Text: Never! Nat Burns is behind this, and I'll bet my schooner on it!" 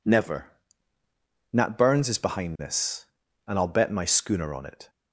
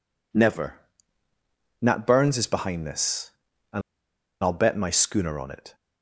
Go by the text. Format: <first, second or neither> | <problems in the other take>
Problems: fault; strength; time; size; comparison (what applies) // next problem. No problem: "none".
first | pauses between "and" and "I'll"; noticeable; at 3.8 s; 0.61 s long